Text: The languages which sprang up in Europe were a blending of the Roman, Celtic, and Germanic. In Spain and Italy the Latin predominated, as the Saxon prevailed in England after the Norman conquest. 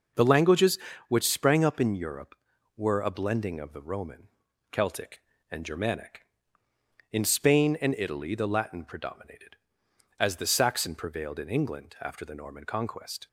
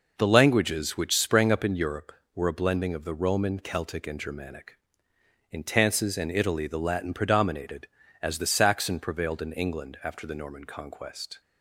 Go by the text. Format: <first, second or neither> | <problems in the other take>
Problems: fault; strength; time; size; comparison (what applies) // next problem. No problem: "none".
first | says "Tances" for "Spain"; at 5.6 s